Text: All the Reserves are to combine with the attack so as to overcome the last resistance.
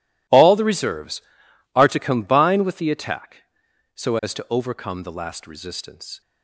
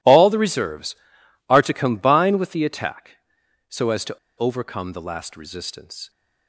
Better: first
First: none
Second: pauses between "to" and "overcome"; slight; at 4.1 s; 0.20 s long

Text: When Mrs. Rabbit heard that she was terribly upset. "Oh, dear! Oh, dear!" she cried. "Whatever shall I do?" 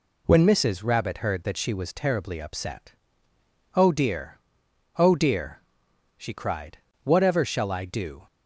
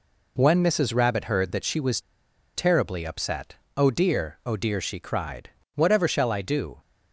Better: first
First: none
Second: pauses between "was" and "terribly"; noticeable; at 1.9 s; 0.56 s long

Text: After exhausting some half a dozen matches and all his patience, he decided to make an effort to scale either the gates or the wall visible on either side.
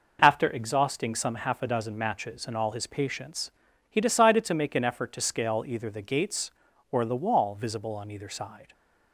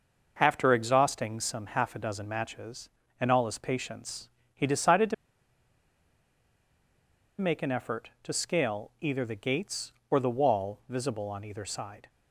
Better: first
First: none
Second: pauses between "to" and "make"; strong; at 5.1 s; 2.2 s long

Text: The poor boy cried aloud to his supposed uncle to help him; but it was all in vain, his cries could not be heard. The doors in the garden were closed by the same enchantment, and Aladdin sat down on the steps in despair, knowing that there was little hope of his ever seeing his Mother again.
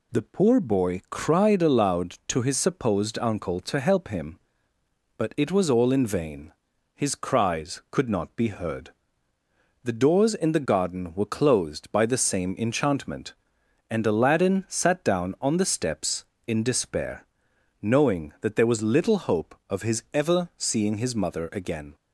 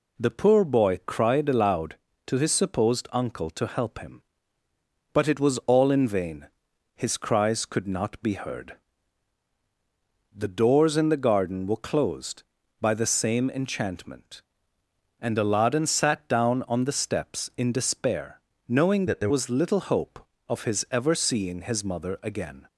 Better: first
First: none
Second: changes voice from "that" to "there"; from 19.0 to 19.3 s; 0.3 s long

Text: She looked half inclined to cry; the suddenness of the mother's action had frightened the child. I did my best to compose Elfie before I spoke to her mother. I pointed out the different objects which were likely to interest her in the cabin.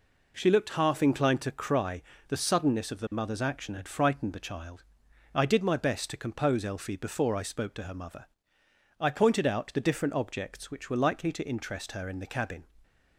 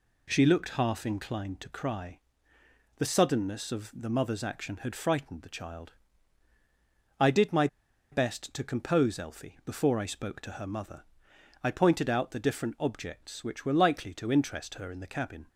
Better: first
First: none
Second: pauses between "my" and "best"; at 7.6 s; 0.45 s long

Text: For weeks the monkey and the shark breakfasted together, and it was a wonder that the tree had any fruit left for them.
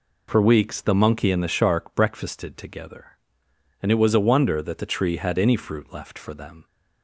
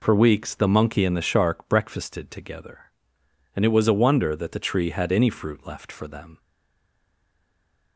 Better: first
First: none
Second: stays silent after the last word; noticeable; from 6.3 s on; 1.6 s long

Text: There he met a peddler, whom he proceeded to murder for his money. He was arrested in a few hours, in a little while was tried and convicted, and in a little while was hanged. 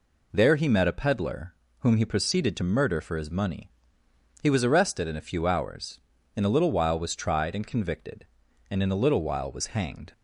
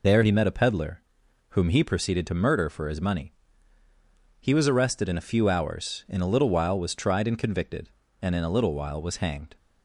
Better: first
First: none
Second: loses the start of "There"; at 0.0 s; 105 ms

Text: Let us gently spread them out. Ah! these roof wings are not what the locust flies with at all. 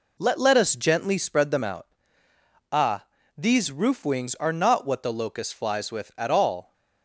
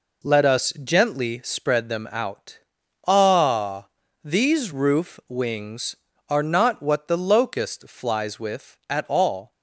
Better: second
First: says "Let" twice; at 0.3 s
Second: none

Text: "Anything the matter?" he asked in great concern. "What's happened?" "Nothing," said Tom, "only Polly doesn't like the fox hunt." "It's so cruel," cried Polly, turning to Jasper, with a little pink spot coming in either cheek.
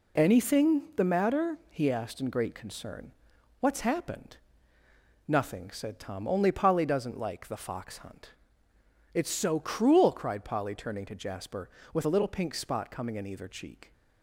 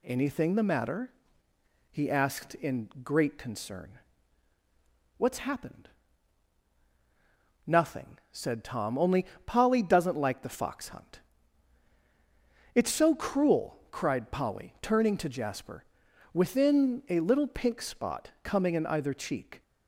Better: first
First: none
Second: pauses between "only" and "Polly"; slight; at 9.2 s; 0.20 s long // says "within" for "with"; at 16.3 s

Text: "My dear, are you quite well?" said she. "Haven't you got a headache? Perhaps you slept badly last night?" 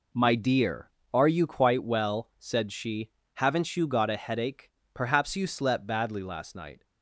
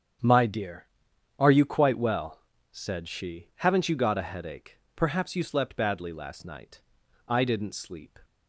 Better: first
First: none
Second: starts louder than the rest; strong; until 1.7 s; 8 dB // goes on to say "I didn't sleep"; noticeable; from 7.2 s on; 0.90 s long

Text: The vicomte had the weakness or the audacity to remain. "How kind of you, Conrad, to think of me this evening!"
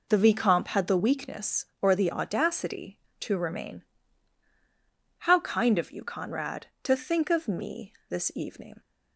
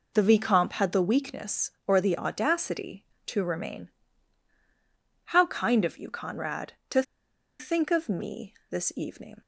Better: first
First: pauses between "me" and "this"; slight; at 7.9 s; 0.16 s long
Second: pauses between "to" and "think"; noticeable; at 7.0 s; 0.57 s long // pauses between "me" and "this"; slight; at 8.5 s; 0.16 s long

